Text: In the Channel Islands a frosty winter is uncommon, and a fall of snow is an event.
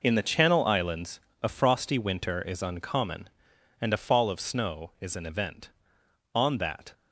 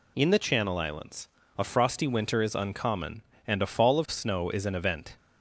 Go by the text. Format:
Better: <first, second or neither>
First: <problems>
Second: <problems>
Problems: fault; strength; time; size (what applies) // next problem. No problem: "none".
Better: second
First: pauses between "Islands" and "a"; slight; at 1.2 s; 0.24 s long // goes on to say "On that"; from 6.3 s on; 0.60 s long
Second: pauses between "Islands" and "a"; slight; at 1.2 s; 0.28 s long